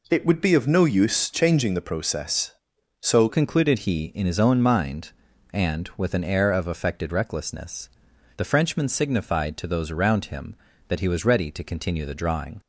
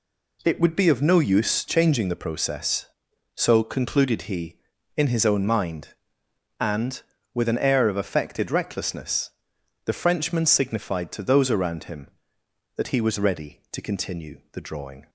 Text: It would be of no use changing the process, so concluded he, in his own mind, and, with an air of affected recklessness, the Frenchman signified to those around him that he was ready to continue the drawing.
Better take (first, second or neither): second